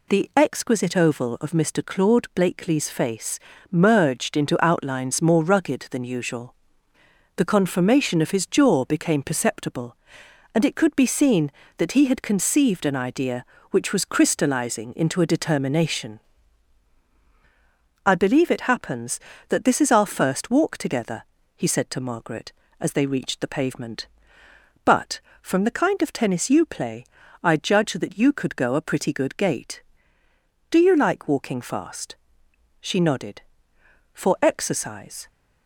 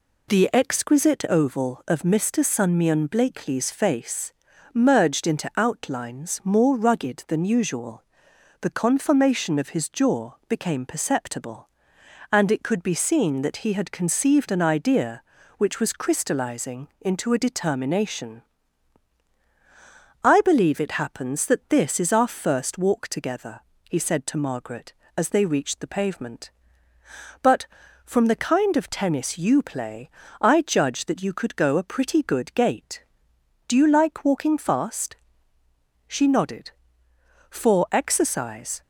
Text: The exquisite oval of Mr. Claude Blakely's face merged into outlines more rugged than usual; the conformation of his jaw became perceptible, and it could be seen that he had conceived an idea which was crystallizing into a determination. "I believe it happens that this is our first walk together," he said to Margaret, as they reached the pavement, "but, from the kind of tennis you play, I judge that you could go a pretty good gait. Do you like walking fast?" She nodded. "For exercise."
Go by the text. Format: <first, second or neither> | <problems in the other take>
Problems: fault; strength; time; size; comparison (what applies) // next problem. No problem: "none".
first | says "Sunmion" for "Claude"; at 2.4 s // pauses between "face" and "merged"; at 4.3 s; 0.44 s long; slight in the first